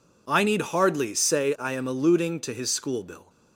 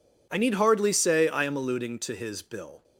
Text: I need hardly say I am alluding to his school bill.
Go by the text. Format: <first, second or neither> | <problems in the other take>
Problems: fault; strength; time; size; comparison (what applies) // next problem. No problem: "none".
first | skips "school"; at 2.4 s